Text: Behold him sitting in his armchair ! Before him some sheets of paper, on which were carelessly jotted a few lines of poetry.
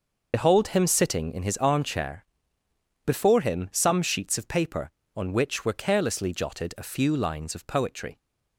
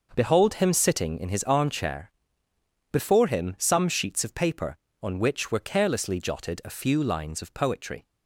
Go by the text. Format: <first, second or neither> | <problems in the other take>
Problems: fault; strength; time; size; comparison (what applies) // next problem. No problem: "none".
second | loses the start of "Behold"; at 0.3 s; 95 ms